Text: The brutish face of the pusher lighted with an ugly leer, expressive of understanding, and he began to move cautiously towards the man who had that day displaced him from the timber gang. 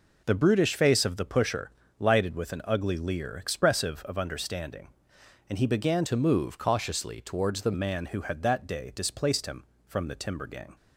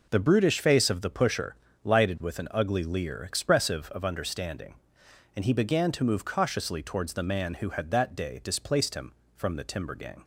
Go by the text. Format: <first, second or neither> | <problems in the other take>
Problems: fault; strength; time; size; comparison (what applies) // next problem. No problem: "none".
second | pauses between "pusher" and "lighted"; slight; at 1.7 s; 0.26 s long; slight in the second // changes voice from "to" to "the"; from 6.0 to 7.7 s; 1.7 s long